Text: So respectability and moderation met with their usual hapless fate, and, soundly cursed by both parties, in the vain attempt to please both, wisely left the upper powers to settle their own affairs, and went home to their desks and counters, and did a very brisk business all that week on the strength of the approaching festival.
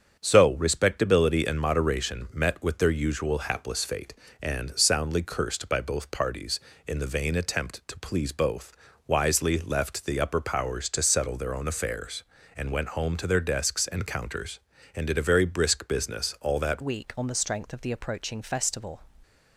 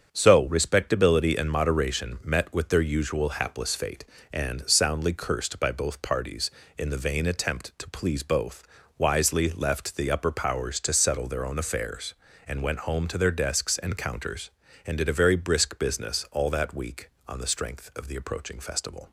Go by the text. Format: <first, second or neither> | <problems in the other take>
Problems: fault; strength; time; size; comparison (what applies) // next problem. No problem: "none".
second | starts louder than the rest; strong; until 1.2 s; 7.5 dB; strong in the second // changes voice at "week"; from 16.8 s on; 2.2 s long